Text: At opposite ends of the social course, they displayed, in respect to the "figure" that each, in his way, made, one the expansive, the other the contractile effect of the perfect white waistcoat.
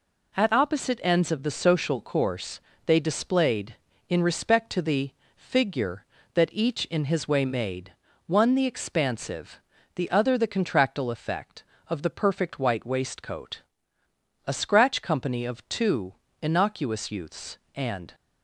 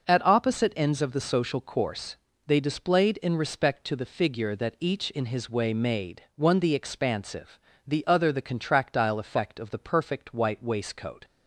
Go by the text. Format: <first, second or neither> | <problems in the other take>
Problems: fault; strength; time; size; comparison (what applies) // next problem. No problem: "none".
second | pauses between "the" and "figure"; slight; at 5.1 s; 0.24 s long // goes on to say "A scratch company of two innocuous youths and"; strong; from 14.4 s on; 3.6 s long